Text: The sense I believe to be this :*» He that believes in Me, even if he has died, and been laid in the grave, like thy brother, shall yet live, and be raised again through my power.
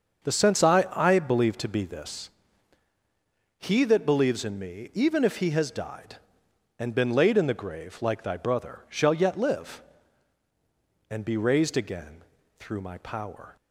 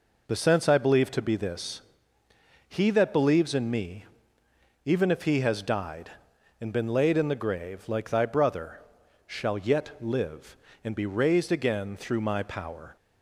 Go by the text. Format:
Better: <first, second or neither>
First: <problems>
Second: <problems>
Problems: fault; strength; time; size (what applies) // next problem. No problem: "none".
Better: second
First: starts louder than the rest; until 1.3 s; 6.5 dB // says "I" twice; at 0.9 s // pauses between "again" and "through"; at 12.2 s; 0.38 s long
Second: none